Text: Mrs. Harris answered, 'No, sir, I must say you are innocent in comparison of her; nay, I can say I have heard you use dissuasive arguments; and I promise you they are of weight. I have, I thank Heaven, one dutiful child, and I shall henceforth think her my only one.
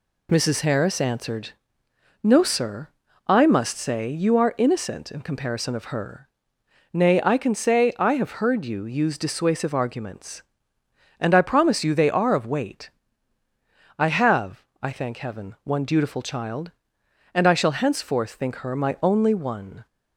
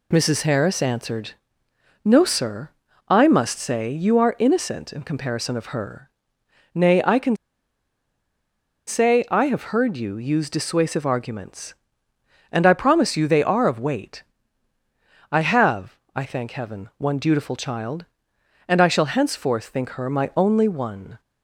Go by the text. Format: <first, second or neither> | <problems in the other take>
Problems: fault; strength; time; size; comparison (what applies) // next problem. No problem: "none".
first | pauses between "can" and "say"; strong; at 7.3 s; 1.5 s long